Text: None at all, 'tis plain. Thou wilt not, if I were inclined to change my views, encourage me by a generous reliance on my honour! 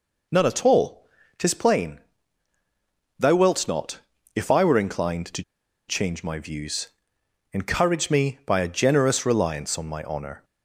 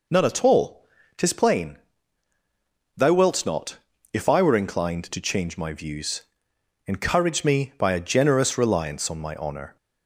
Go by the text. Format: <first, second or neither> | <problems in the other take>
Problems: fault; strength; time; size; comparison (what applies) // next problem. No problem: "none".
second | pauses between "to" and "change"; at 5.4 s; 0.45 s long